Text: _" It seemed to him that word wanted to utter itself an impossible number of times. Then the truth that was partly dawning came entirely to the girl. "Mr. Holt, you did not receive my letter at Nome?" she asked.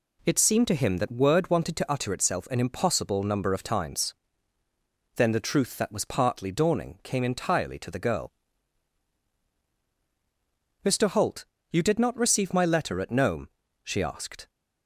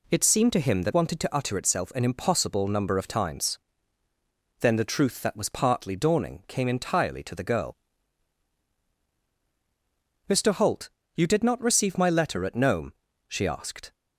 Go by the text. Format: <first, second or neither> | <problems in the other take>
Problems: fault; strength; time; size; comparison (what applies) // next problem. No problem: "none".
first | skips "word"; at 0.9 s